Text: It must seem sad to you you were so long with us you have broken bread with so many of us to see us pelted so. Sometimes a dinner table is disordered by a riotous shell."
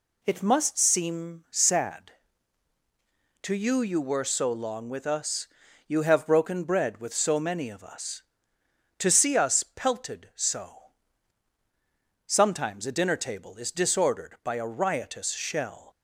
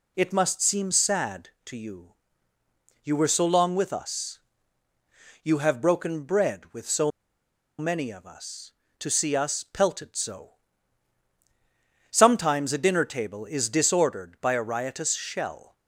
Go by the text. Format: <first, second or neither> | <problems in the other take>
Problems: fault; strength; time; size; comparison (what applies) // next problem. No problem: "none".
first | pauses between "you" and "you"; noticeable; at 2.1 s; 0.90 s long // pauses between "us" and "you"; at 4.3 s; 1.0 s long; also in the first // pauses between "so" and "many"; noticeable; at 7.1 s; 0.68 s long